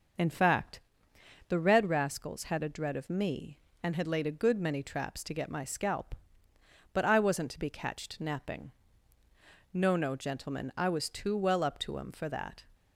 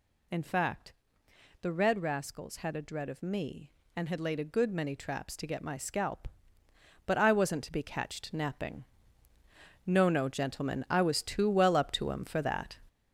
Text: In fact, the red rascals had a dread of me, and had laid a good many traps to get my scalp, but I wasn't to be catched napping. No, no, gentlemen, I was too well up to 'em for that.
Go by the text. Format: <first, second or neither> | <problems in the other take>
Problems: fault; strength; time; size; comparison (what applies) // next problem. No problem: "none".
first | gets louder; strong; throughout; 7 dB